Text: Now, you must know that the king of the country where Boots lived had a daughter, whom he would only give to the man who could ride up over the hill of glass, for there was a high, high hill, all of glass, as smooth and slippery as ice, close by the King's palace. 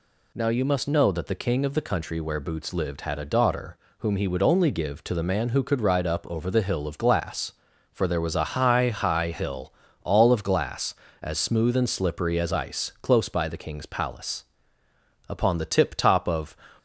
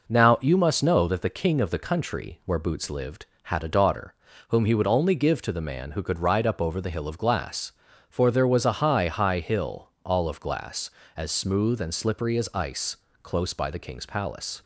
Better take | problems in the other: second | goes on to say "Upon the tip top of"; noticeable; from 15.2 s on; 1.2 s long

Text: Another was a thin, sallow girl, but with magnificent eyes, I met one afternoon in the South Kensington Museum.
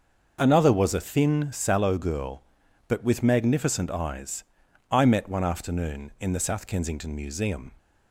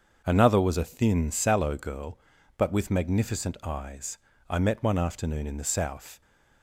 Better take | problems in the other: first | starts louder than the rest; until 1.2 s; 6.5 dB; also in the first // stops before "Kensington Museum"; at 6.2 s

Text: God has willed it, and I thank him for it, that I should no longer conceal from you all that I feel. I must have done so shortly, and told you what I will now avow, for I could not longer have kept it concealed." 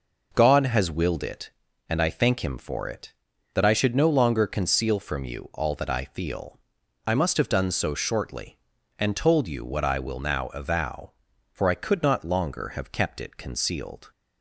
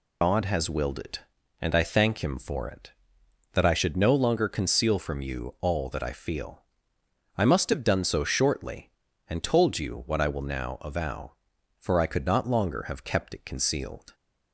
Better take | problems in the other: first | loses the start of "God"; at 0.2 s; 95 ms

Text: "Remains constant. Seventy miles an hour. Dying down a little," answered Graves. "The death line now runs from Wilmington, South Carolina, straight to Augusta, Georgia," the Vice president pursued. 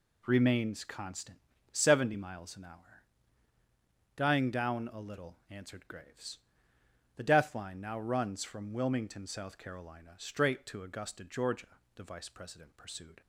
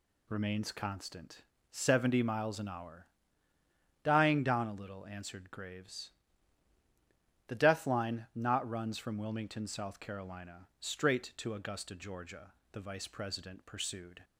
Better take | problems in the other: first | says "not" for "now"; at 8.3 s

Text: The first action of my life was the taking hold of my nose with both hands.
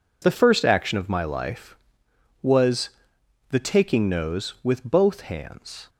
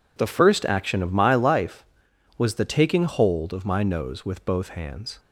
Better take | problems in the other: second | pauses between "was" and "the"; noticeable; at 2.9 s; 0.58 s long // skips "hold of my"; at 4.0 s

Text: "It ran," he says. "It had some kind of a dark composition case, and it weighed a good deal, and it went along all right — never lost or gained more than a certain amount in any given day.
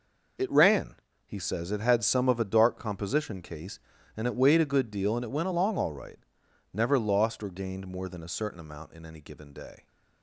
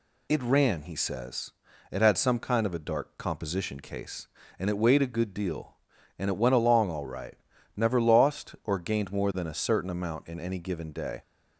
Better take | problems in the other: second | skips "kind"; at 2.2 s

